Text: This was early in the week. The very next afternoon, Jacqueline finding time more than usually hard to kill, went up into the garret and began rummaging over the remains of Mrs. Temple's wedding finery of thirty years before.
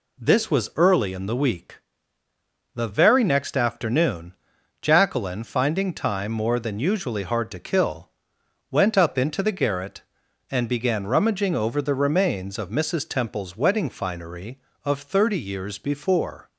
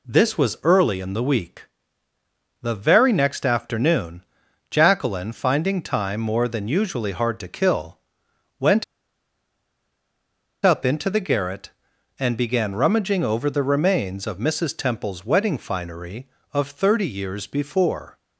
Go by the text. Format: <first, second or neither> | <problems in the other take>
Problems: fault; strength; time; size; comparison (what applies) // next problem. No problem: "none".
first | pauses between "went" and "up"; strong; at 8.8 s; 1.7 s long